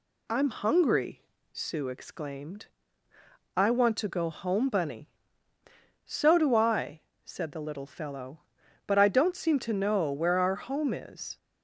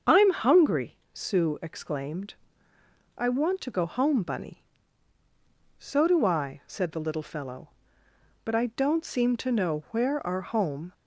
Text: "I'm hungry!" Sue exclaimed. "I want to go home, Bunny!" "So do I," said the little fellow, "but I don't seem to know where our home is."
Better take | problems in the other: first | starts louder than the rest; until 1.2 s; 7 dB // stops before "is"; at 10.9 s

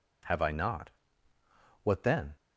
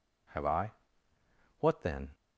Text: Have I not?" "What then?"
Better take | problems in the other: first | skips "not"; at 1.1 s

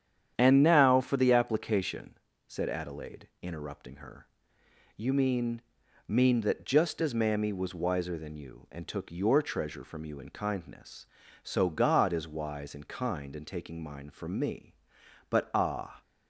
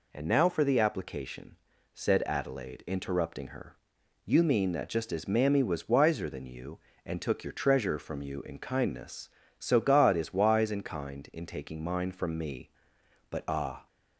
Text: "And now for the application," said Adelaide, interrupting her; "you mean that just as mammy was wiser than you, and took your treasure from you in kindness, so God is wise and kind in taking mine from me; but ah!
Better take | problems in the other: second | starts louder than the rest; strong; until 1.3 s; 9 dB // says "mean" twice; at 6.0 s

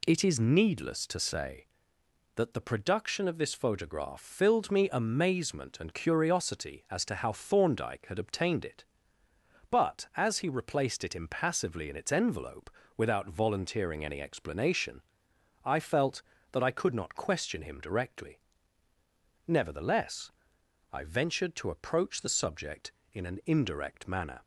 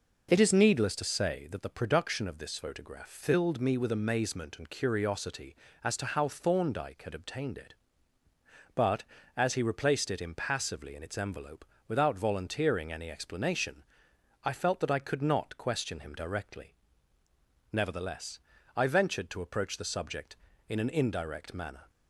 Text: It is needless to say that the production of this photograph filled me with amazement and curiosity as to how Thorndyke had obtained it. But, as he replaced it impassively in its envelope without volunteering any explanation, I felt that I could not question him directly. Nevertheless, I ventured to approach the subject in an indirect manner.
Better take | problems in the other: second | skips "with"; at 4.9 s // pauses between "envelope" and "without"; slight; at 12.6 s; 0.28 s long; slight in the second

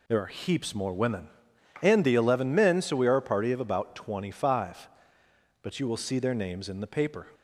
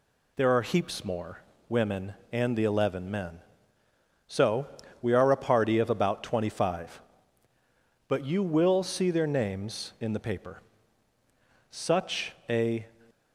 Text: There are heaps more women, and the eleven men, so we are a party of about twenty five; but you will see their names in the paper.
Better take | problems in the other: first | pauses between "more" and "women"; slight; at 1.3 s; 0.28 s long // pauses between "so" and "we"; slight; at 4.6 s; 0.34 s long // goes on to say "Such a"; noticeable; from 11.6 s on; 1.1 s long

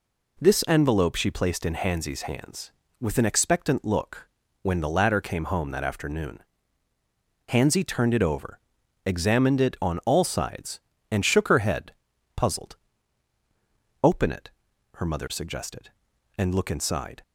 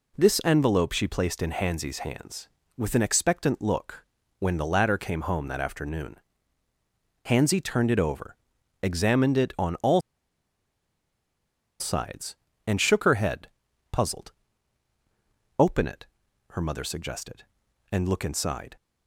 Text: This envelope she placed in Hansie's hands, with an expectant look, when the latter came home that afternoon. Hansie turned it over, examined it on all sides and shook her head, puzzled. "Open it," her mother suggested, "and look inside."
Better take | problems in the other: first | pauses between "all" and "sides"; strong; at 9.9 s; 1.8 s long

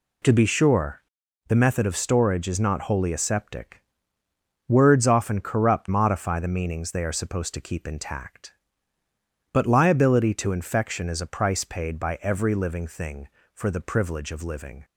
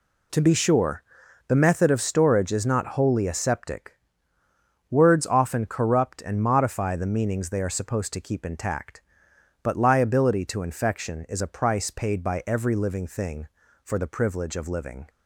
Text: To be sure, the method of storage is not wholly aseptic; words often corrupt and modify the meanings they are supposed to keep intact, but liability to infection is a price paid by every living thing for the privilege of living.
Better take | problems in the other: second | skips "and"; at 5.9 s

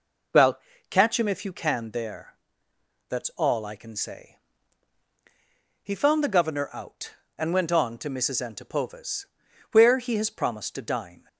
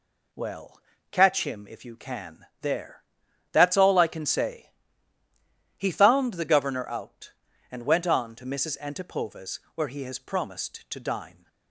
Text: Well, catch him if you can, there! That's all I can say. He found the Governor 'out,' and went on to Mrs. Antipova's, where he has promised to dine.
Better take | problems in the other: neither | none

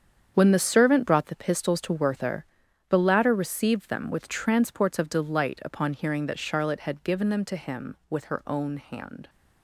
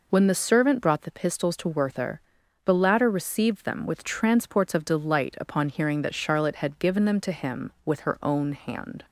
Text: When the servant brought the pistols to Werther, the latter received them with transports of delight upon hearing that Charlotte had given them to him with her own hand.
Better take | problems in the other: second | gets quieter; strong; throughout; 12 dB

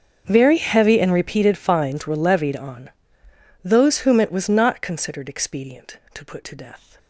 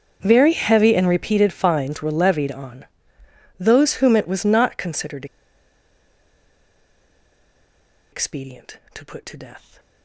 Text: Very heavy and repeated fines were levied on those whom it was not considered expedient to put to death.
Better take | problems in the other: first | starts louder than the rest; until 1.2 s; 7 dB; also in the first // pauses between "on" and "those"; noticeable; at 2.8 s; 0.74 s long; noticeable in the first // pauses between "considered" and "expedient"; strong; at 5.2 s; 2.8 s long

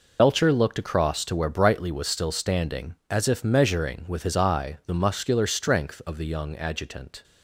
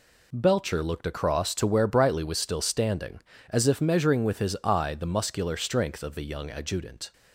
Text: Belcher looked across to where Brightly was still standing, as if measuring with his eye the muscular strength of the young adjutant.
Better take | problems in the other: second | loses the start of "Belcher"; at 0.1 s; 50 ms

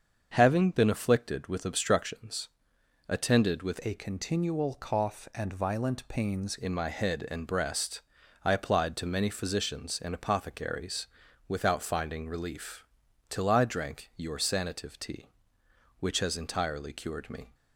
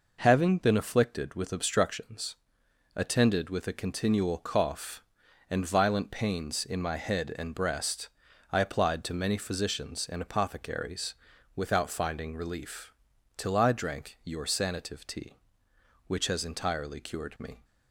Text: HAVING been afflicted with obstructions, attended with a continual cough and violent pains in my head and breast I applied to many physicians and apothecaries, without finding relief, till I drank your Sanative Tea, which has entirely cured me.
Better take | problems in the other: second | starts louder than the rest; until 1.3 s; 6.5 dB // changes voice from "a" to "pains"; from 3.8 to 6.5 s; 2.7 s long // pauses between "breast" and "I"; at 8.0 s; 0.42 s long; also in the second

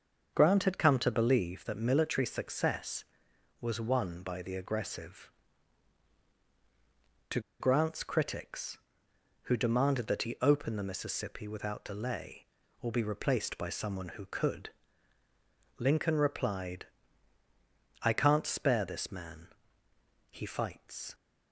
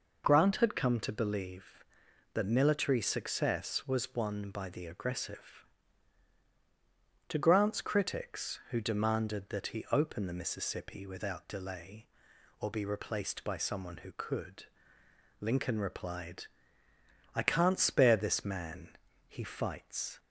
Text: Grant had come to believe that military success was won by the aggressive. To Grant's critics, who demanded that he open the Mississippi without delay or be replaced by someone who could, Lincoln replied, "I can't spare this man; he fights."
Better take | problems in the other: second | starts louder than the rest; until 1.3 s; 6.5 dB // pauses between "To" and "Grant's"; slight; at 7.4 s; 0.19 s long

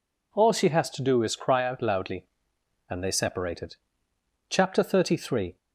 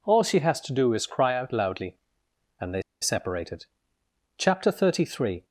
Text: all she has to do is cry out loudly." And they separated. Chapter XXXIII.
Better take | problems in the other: first | pauses between "they" and "separated"; slight; at 2.8 s; 0.19 s long

